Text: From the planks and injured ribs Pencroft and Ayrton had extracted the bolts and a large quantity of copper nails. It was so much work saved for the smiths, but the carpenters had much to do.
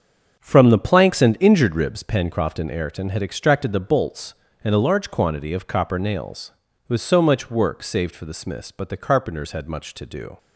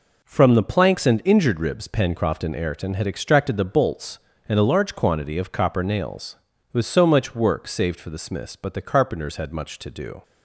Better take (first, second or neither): second